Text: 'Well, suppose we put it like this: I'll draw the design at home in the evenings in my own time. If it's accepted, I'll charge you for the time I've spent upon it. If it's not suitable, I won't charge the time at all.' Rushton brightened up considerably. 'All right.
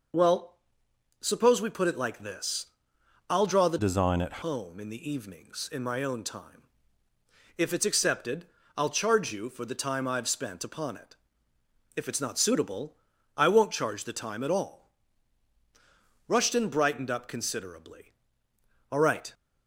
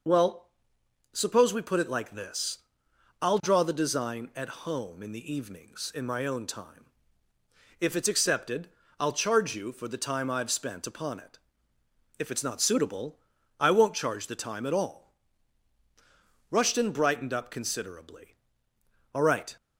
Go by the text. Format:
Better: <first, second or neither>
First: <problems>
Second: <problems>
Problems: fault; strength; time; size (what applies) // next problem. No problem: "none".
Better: second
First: changes voice from "design" to "at"; from 3.7 to 4.4 s; 0.7 s long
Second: none